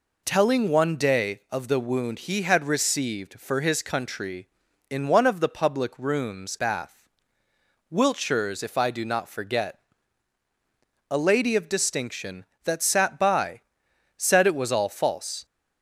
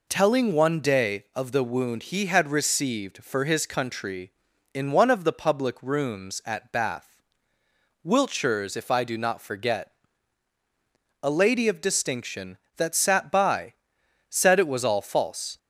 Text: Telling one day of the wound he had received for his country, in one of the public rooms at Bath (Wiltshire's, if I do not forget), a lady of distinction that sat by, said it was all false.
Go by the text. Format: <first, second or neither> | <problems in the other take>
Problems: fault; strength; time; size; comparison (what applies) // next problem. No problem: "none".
second | skips "at"; at 6.5 s